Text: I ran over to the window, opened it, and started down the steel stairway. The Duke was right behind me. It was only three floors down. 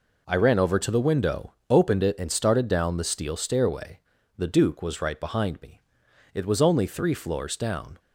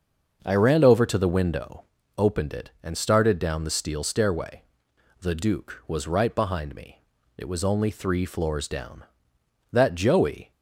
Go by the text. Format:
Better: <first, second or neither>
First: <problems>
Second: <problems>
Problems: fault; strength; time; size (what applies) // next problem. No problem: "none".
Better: first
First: none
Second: starts louder than the rest; until 1.4 s; 6.5 dB // goes on to say "That Joey"; noticeable; from 9.7 s on; 0.80 s long